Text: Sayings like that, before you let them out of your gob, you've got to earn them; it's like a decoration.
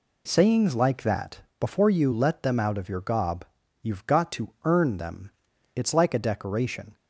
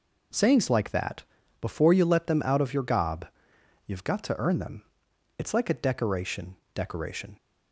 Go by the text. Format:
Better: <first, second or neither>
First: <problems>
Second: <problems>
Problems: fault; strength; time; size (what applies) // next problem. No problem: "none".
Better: first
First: none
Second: says "decoration" twice; at 6.7 s